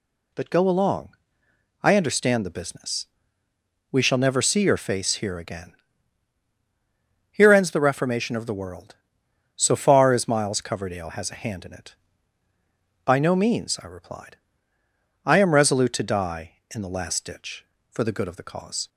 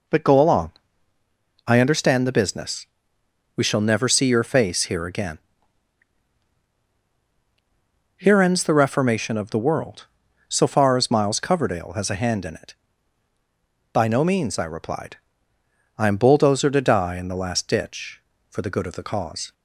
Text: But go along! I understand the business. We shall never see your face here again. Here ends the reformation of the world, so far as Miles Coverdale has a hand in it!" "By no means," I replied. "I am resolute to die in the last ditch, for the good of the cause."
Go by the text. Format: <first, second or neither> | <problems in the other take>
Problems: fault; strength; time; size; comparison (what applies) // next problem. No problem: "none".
first | says "bulldozer" for "resolute"; at 16.1 s